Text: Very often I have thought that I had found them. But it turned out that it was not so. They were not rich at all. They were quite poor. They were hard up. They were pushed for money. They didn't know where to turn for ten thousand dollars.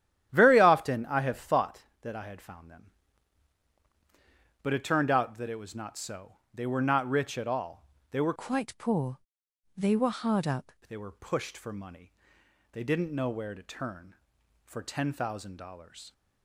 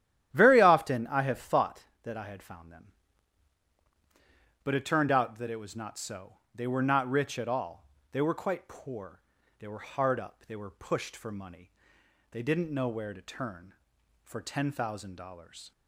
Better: second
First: starts louder than the rest; strong; until 1.3 s; 11.5 dB // changes voice from "quite" to "up"; from 8.3 to 10.7 s; 2.4 s long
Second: starts louder than the rest; strong; until 1.3 s; 12 dB

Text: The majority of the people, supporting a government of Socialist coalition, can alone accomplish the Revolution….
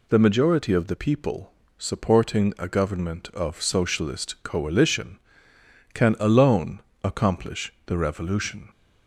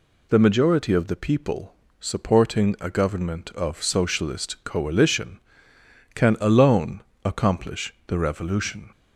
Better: neither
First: pauses between "alone" and "accomplish"; slight; at 6.8 s; 0.20 s long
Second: pauses between "alone" and "accomplish"; slight; at 7.0 s; 0.20 s long

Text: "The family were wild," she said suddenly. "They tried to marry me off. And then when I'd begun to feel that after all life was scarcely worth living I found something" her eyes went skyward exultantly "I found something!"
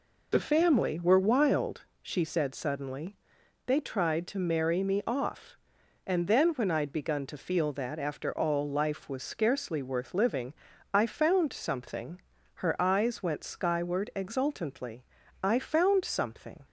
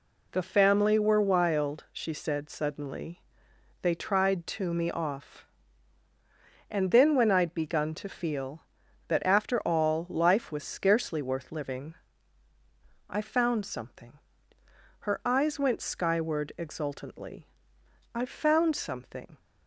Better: first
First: pauses between "living" and "I"; at 10.5 s; 0.40 s long // pauses between "something" and "her"; slight; at 12.2 s; 0.34 s long // pauses between "exultantly" and "I"; slight; at 15.0 s; 0.36 s long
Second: skips "marry"; at 4.7 s // pauses between "living" and "I"; at 11.9 s; 1.1 s long // pauses between "something" and "her"; noticeable; at 14.1 s; 0.82 s long // pauses between "exultantly" and "I"; noticeable; at 17.4 s; 0.68 s long

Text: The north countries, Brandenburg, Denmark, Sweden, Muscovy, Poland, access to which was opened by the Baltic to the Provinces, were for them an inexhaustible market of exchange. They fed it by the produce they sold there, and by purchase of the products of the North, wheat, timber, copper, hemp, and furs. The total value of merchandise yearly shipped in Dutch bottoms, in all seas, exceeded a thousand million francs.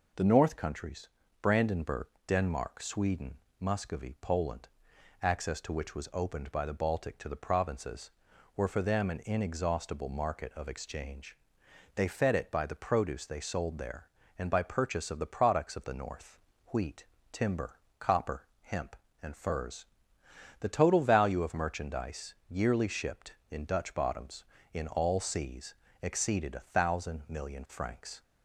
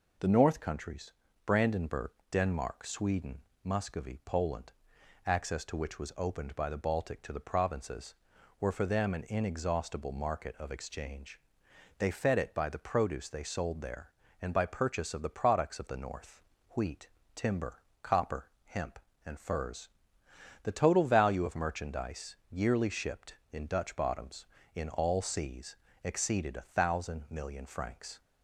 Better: neither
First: none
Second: none

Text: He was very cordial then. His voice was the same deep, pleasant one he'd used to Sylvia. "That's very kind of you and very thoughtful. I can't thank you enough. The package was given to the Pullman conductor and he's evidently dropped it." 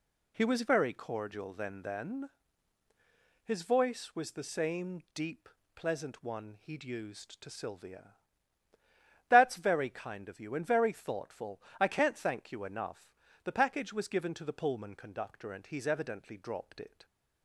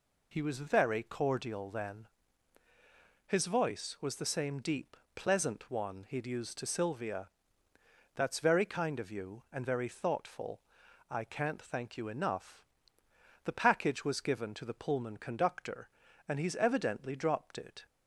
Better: second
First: says "then" twice; at 1.8 s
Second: none

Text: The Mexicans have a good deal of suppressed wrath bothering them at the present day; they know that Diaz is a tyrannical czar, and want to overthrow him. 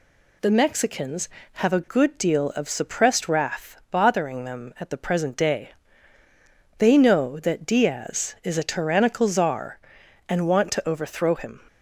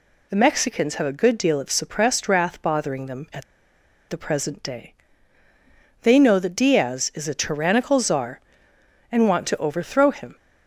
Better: first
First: none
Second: pauses between "at" and "the"; noticeable; at 3.4 s; 0.65 s long

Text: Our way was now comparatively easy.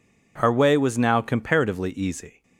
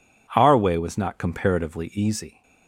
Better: first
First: none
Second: says "not" for "now"; at 0.9 s

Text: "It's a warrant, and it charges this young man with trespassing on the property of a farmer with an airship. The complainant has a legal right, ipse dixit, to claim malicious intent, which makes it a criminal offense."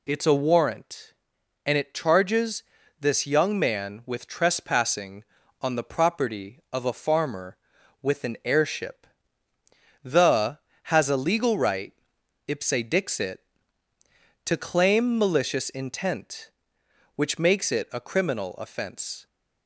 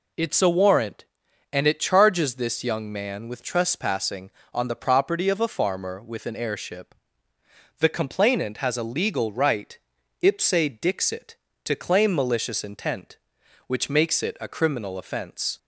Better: second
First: pauses between "charges" and "this"; slight; at 2.6 s; 0.34 s long // skips "complainant"; at 10.7 s // pauses between "ipse" and "dixit"; slight; at 12.6 s; 0.18 s long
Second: pauses between "ipse" and "dixit"; slight; at 10.5 s; 0.28 s long

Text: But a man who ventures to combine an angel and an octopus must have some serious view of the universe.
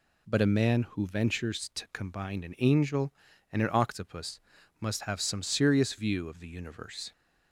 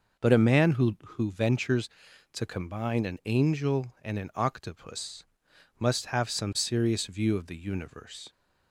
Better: first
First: pauses between "octopus" and "must"; at 4.3 s; 0.40 s long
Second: says "who" twice; at 1.0 s // pauses between "octopus" and "must"; noticeable; at 5.2 s; 0.56 s long

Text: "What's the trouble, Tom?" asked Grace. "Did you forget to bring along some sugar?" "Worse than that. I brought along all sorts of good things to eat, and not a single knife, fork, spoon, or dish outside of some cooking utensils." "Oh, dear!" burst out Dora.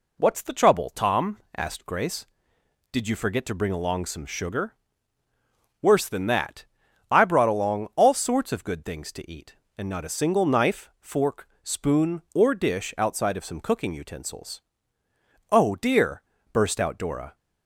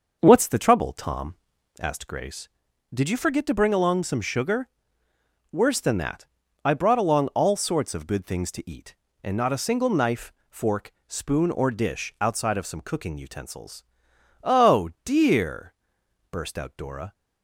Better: first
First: none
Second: starts louder than the rest; noticeable; until 2.0 s; 6 dB

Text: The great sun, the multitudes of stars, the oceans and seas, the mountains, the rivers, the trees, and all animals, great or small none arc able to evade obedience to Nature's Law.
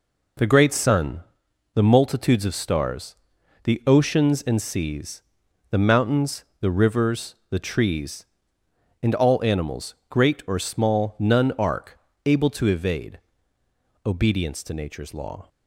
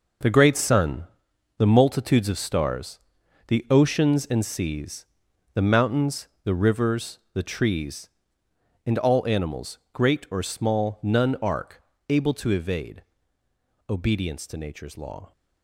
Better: first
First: pauses between "arc" and "able"; slight; at 11.9 s; 0.26 s long // pauses between "evade" and "obedience"; noticeable; at 13.1 s; 0.88 s long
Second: gets quieter; strong; throughout; 9.5 dB // pauses between "arc" and "able"; slight; at 11.8 s; 0.26 s long // pauses between "evade" and "obedience"; noticeable; at 13.0 s; 0.88 s long

